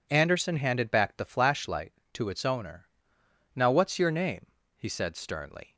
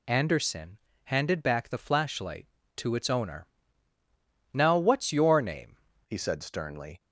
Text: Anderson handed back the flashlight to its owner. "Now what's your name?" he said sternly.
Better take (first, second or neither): first